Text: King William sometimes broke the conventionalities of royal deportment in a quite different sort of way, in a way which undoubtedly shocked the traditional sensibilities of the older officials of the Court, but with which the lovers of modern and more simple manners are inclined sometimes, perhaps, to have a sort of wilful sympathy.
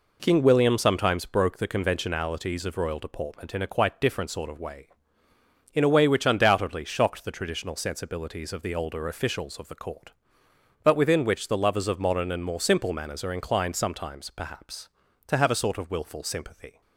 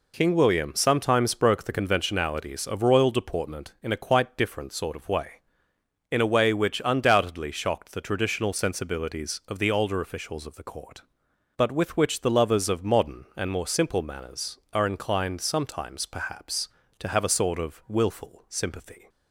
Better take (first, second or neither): second